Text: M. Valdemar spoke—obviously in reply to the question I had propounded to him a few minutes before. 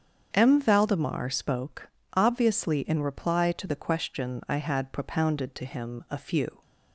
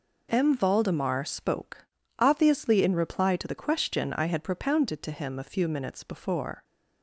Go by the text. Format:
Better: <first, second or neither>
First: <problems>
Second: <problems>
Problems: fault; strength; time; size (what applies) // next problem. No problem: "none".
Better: second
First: starts louder than the rest; strong; until 1.3 s; 7.5 dB // stops before "minutes before"; at 6.6 s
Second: none